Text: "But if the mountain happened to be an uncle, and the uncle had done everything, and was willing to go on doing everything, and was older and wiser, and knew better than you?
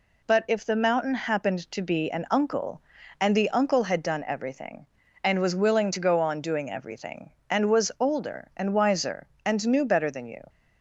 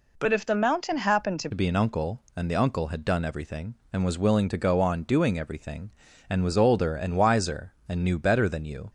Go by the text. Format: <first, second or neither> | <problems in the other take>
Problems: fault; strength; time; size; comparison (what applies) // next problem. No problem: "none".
first | changes voice at "be"; from 1.5 s on; 7.4 s long